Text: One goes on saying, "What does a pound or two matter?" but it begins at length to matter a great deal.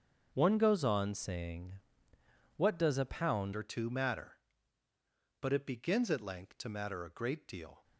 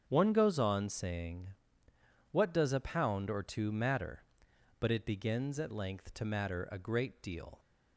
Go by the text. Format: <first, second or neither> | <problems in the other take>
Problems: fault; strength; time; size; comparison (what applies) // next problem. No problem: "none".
second | starts louder than the rest; until 1.3 s; 7 dB; strong in the second // changes voice at "or"; from 3.5 s on; 4.3 s long